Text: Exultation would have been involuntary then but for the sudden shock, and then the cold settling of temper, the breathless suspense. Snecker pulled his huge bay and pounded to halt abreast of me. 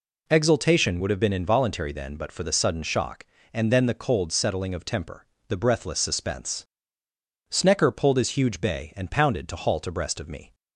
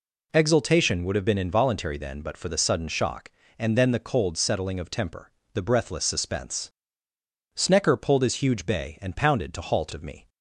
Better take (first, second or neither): first